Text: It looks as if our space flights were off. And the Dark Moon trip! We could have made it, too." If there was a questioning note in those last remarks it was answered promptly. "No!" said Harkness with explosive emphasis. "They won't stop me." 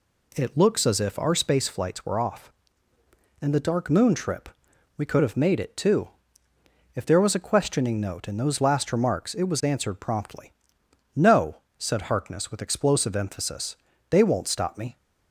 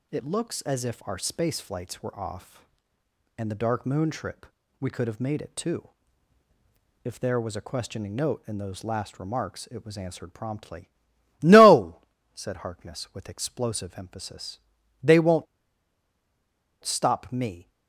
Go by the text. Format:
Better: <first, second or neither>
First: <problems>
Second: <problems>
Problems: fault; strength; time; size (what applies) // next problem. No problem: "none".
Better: first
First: none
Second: pauses between "won't" and "stop"; strong; at 15.4 s; 1.3 s long